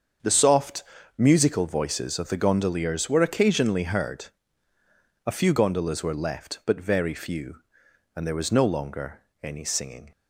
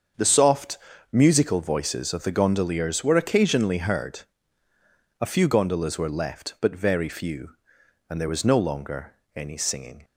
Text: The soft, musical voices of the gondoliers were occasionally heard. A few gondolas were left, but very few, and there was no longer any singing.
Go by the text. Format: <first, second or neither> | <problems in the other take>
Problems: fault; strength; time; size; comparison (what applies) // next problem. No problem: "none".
neither | starts louder than the rest; the same in both // pauses between "longer" and "any"; slight; the same in both